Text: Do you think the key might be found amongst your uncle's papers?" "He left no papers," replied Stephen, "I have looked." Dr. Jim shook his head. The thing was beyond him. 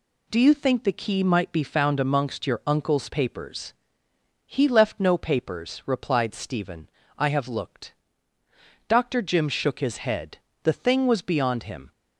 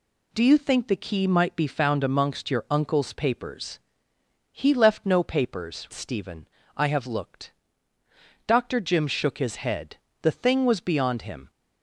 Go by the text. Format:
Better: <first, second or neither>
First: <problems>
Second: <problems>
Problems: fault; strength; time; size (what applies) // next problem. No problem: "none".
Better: first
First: none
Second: skips "replied"; at 5.9 s